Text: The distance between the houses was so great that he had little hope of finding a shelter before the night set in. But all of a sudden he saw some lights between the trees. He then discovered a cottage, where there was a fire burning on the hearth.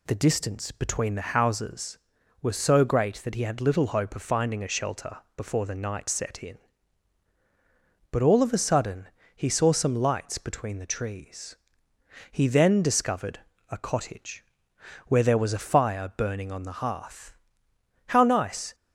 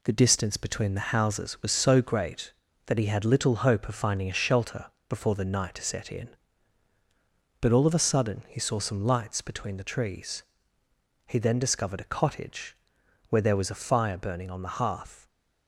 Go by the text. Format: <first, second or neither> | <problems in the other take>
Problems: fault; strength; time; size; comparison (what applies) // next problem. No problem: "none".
second | pauses between "shelter" and "before"; slight; at 5.1 s; 0.16 s long; slight in the second // pauses between "sudden" and "he"; slight; at 9.0 s; 0.26 s long // pauses between "discovered" and "a"; slight; at 13.4 s; 0.28 s long // goes on to say "How nice"; noticeable; from 18.0 s on; 0.68 s long